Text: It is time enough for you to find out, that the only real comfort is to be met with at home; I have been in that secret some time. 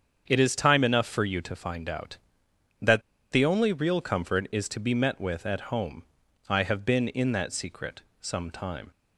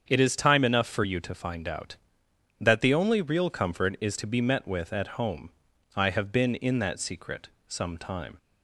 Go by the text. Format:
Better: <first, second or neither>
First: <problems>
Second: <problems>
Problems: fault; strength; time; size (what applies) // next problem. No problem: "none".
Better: second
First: starts louder than the rest; strong; until 1.2 s; 7.5 dB // pauses between "that" and "the"; slight; at 3.0 s; 0.31 s long // pauses between "secret" and "some"; slight; at 8.0 s; 0.22 s long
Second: starts louder than the rest; strong; until 1.0 s; 7.5 dB // pauses between "secret" and "some"; slight; at 7.4 s; 0.22 s long